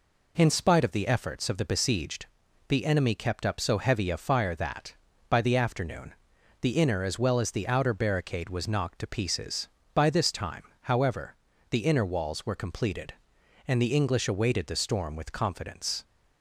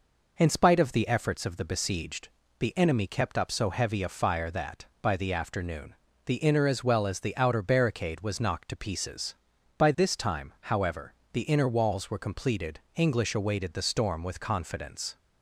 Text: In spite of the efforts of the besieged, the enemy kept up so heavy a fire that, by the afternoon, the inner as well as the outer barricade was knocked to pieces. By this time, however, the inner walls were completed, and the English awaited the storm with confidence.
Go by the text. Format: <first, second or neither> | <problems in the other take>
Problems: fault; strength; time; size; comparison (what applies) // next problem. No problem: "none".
first | skips "and the"; at 12.8 s